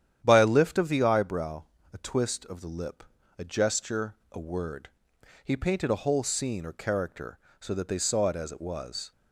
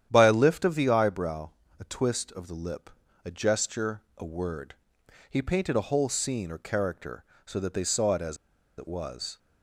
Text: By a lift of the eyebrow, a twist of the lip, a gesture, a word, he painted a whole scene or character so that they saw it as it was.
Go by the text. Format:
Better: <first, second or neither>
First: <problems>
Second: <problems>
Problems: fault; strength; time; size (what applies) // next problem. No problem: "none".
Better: first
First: starts louder than the rest; strong; until 1.2 s; 10 dB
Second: starts louder than the rest; strong; until 1.1 s; 10 dB // pauses between "as" and "it"; at 8.3 s; 0.41 s long